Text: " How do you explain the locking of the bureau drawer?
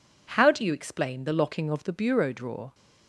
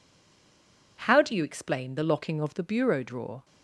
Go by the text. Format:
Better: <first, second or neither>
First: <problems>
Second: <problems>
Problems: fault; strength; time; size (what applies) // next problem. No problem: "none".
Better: first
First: none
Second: stays silent before the first word; until 0.9 s; 0.9 s long